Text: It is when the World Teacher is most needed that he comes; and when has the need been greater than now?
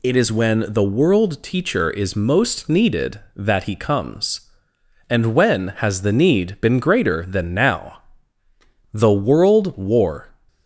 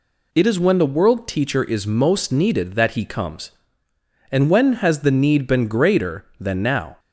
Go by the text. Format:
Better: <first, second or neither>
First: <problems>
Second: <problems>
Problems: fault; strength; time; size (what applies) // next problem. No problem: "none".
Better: second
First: goes on to say "The world war"; from 8.9 s on; 1.3 s long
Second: none